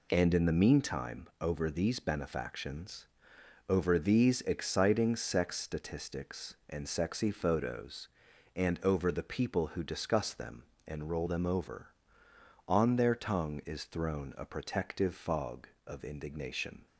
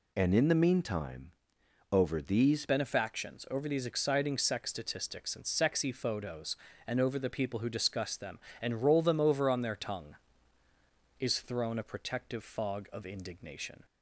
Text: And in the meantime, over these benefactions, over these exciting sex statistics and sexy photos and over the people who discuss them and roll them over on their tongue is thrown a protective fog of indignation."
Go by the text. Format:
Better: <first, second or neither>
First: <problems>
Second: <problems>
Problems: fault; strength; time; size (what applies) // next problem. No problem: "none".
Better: first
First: none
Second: changes voice at "benefactions"; from 2.6 s on; 11.2 s long